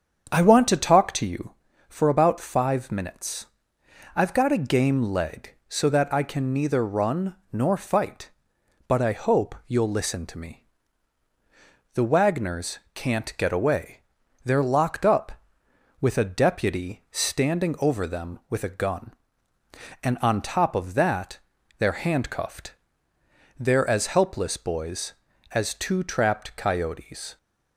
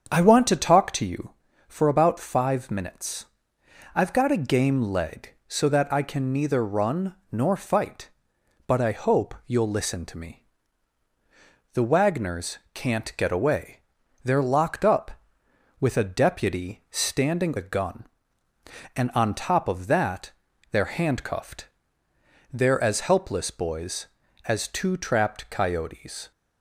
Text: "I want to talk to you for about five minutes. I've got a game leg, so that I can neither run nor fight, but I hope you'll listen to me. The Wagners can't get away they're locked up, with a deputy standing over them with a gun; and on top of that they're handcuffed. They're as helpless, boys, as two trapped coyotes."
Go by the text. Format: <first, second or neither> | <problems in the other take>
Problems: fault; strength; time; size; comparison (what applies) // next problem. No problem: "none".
first | starts louder than the rest; strong; until 1.1 s; 7 dB; strong in the first // pauses between "Wagners" and "can't"; slight; at 12.5 s; 0.16 s long; slight in the first // pauses between "away" and "they're"; at 13.7 s; 0.44 s long; also in the first // skips "over them with"; at 17.5 s // pauses between "that" and "they're"; at 20.3 s; 0.40 s long; also in the first